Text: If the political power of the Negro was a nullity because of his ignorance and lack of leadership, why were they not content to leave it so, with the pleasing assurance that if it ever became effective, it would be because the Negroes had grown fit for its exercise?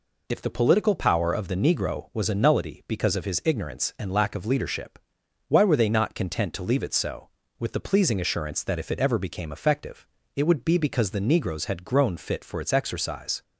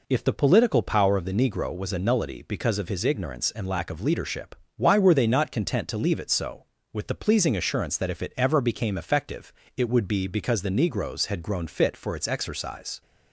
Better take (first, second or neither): neither